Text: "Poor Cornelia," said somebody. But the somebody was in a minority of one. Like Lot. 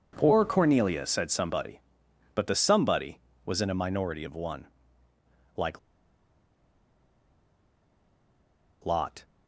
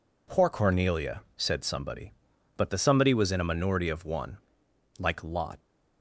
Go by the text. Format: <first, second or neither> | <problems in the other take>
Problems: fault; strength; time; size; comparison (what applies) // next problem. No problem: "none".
second | pauses between "Like" and "Lot"; strong; at 5.7 s; 3.0 s long